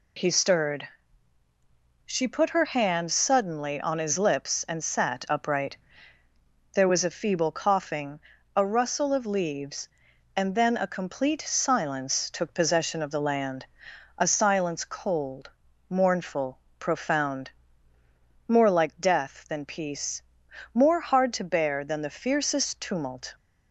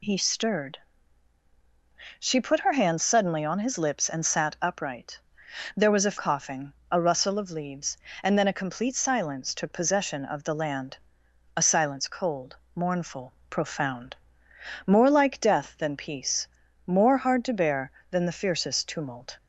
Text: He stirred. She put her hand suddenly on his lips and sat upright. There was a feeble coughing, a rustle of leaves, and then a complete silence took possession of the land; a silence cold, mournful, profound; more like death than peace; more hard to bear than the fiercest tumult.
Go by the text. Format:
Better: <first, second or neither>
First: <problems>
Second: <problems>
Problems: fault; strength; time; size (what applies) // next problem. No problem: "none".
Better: first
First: none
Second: skips "feeble"; at 6.1 s